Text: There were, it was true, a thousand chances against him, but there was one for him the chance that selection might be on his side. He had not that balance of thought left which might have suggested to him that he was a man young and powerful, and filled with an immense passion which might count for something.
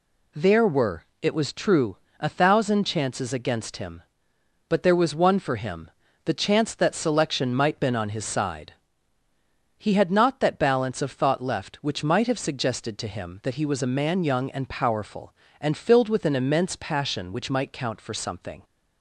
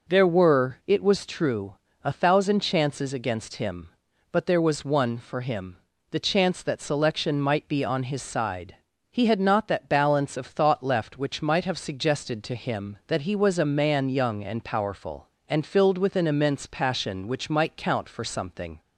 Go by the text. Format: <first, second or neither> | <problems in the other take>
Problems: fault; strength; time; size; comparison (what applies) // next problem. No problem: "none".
second | pauses between "him" and "the"; slight; at 5.8 s; 0.36 s long; slight in the second // says "been" for "be"; at 7.7 s